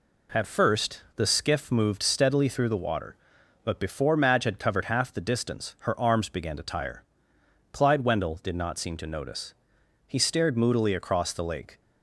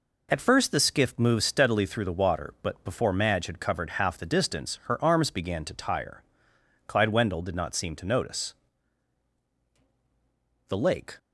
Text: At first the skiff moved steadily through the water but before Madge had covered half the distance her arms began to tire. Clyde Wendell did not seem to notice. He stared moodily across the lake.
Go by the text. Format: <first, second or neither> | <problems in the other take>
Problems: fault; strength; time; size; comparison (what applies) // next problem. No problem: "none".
first | skips "He stared moodily across"; at 9.6 s